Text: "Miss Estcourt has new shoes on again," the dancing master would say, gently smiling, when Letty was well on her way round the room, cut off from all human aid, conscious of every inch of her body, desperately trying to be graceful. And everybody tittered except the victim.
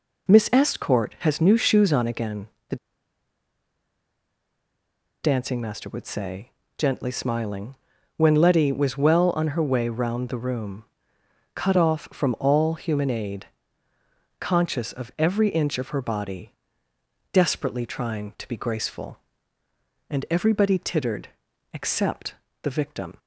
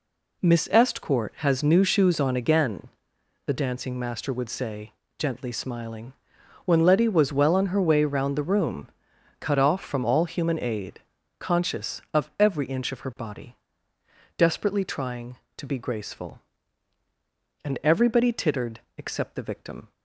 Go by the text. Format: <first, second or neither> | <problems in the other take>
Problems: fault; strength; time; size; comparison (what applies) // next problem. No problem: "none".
second | pauses between "the" and "dancing"; strong; at 2.7 s; 2.4 s long // pauses between "tittered" and "except"; noticeable; at 21.2 s; 0.46 s long; slight in the second // pauses between "except" and "the"; slight; at 22.3 s; 0.26 s long